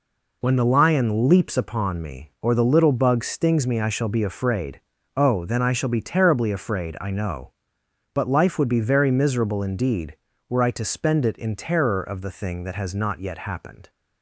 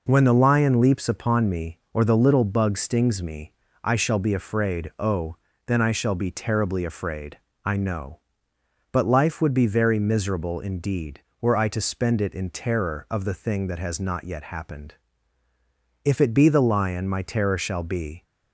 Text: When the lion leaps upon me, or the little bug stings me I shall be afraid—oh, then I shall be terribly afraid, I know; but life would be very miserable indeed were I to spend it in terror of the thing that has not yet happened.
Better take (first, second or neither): first